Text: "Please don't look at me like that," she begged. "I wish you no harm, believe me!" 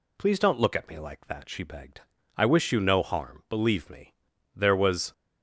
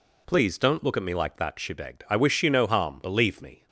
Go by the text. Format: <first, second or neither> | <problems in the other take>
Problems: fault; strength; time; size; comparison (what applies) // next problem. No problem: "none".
second | goes on to say "There was"; from 4.5 s on; 0.58 s long